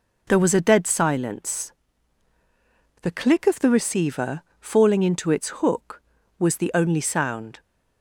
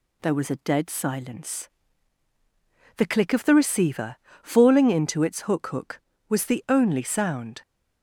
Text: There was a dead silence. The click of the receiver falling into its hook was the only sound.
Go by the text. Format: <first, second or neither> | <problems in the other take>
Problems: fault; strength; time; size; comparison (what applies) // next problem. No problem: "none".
first | pauses between "receiver" and "falling"; slight; at 4.1 s; 0.24 s long; slight in the first // says "hook" twice; at 5.6 s